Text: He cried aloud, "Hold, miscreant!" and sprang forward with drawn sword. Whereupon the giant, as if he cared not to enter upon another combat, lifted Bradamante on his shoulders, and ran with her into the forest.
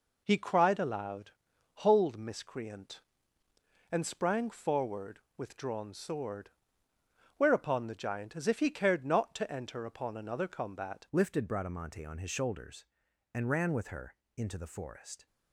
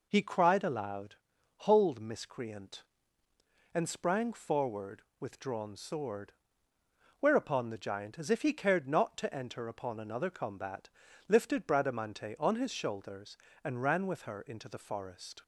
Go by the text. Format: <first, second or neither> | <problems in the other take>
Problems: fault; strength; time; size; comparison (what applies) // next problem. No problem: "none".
second | changes voice at "lifted"; from 11.1 s on; 4.1 s long // pauses between "her" and "into"; slight; at 14.1 s; 0.20 s long